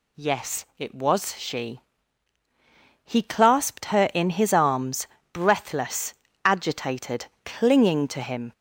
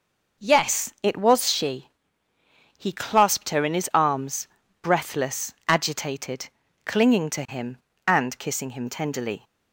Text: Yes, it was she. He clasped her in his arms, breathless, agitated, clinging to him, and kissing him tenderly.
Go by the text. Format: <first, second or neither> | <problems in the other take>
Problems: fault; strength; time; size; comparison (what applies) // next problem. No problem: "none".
second | stops before "and kissing him tenderly"; at 8.5 s